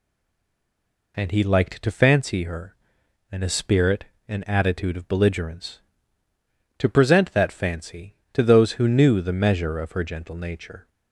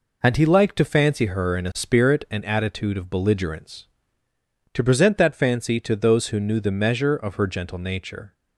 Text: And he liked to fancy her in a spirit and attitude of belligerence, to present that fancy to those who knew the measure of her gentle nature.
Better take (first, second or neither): second